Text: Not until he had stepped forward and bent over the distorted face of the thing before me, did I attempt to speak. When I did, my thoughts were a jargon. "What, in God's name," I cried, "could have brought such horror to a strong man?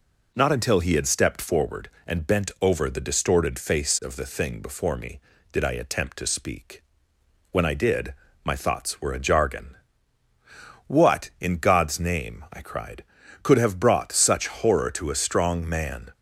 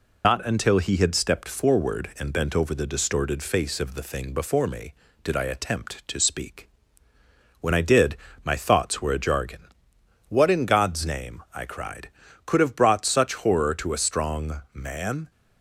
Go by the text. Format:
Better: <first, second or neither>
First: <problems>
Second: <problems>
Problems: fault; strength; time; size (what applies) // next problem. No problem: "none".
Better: first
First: none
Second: loses the start of "Not"; at 0.2 s; 95 ms